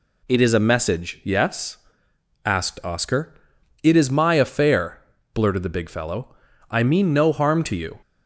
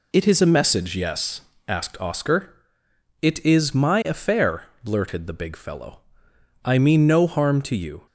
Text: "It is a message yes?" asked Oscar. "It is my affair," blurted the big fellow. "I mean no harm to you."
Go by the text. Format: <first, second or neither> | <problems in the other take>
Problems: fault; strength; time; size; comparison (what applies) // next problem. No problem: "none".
neither | none